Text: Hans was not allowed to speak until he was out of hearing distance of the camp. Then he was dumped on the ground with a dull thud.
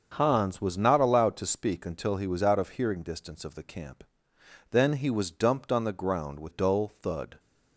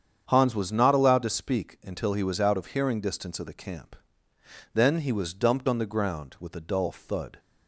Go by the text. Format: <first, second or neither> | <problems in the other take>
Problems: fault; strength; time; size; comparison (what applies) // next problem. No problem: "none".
second | starts louder than the rest; until 1.1 s; 6.5 dB; strong in the second // skips "a"; at 6.5 s